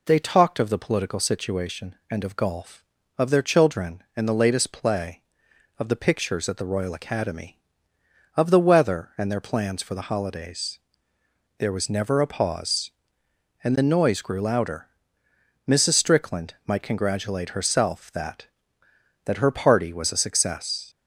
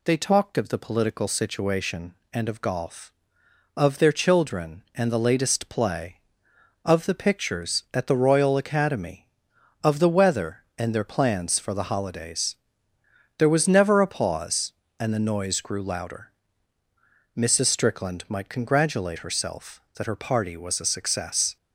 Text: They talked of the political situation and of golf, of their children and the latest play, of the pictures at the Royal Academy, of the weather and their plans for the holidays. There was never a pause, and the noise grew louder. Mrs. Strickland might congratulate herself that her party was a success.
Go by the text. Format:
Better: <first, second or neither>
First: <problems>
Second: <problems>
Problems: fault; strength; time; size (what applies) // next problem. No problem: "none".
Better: second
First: says "that" twice; at 19.2 s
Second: none